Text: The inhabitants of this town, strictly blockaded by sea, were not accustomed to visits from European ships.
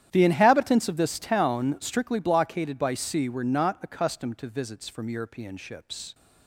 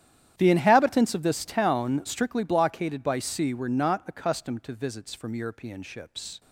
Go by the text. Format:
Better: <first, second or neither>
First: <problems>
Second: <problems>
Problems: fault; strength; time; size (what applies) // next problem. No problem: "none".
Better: neither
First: starts louder than the rest; strong; until 1.1 s; 10.5 dB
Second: starts louder than the rest; strong; until 1.3 s; 10.5 dB